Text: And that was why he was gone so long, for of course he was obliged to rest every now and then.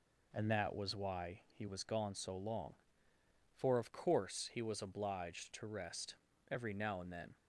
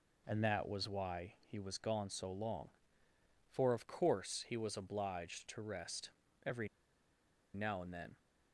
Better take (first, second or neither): first